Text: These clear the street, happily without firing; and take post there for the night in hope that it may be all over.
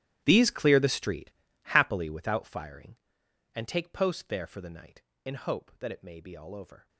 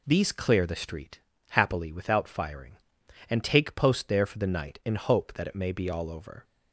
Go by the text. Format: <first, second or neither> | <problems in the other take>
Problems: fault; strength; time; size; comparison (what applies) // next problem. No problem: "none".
second | gets quieter; strong; throughout; 19 dB